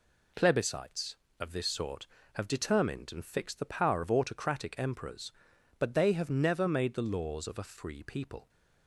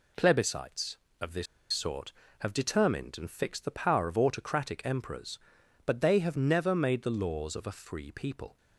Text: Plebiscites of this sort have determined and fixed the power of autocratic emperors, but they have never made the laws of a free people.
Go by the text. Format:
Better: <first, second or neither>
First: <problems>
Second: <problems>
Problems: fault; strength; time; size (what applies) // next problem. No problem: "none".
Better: first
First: none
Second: pauses between "this" and "sort"; slight; at 1.4 s; 0.27 s long